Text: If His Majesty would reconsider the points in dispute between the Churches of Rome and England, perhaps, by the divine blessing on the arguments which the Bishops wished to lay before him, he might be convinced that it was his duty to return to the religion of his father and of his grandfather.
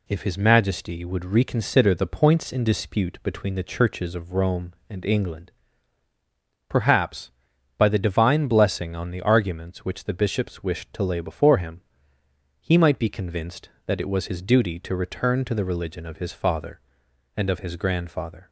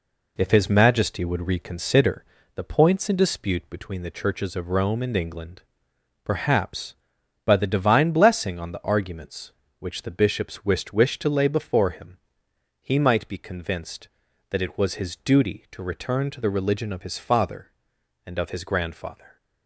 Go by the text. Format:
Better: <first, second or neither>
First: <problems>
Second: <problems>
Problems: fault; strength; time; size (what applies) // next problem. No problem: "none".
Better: first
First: none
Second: pauses between "reconsider" and "the"; slight; at 2.2 s; 0.33 s long // says "wished" twice; at 10.9 s